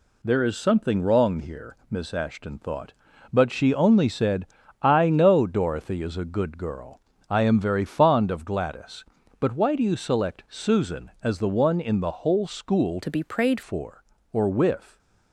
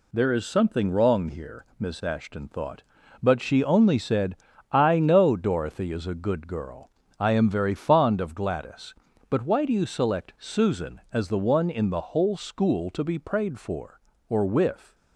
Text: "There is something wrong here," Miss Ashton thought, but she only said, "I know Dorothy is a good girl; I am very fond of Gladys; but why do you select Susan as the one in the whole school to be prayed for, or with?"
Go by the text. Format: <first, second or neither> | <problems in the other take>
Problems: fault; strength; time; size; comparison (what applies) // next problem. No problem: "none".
second | changes voice from "to" to "prayed"; from 13.0 to 13.6 s; 0.6 s long